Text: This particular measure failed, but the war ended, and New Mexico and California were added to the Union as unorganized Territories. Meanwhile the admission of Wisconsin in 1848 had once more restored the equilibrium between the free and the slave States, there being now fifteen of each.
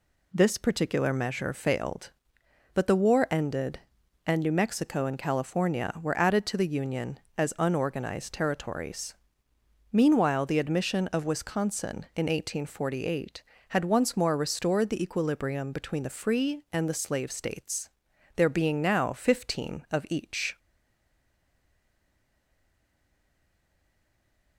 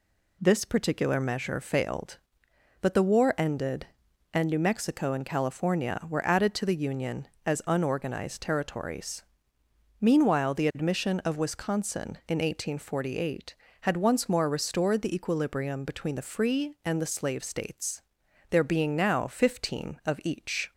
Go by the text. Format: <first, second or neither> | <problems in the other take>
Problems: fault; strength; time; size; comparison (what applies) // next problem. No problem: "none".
second | stays silent after the last word; strong; from 20.5 s on; 4.0 s long